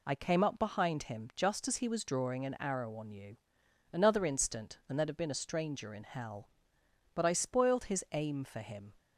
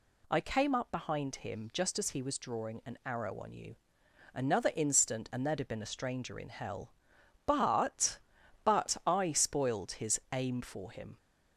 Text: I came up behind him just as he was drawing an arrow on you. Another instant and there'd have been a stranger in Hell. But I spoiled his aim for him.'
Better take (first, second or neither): first